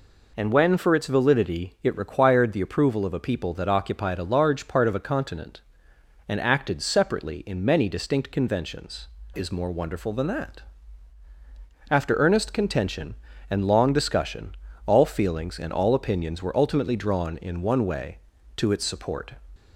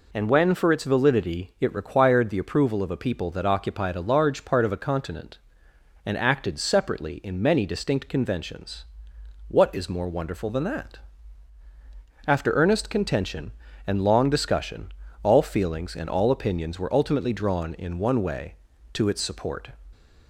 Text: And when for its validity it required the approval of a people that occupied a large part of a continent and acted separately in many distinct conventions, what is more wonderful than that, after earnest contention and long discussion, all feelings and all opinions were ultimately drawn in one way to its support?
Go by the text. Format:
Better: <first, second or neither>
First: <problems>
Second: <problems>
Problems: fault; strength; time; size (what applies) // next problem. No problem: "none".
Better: second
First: skips "what"; at 9.2 s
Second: none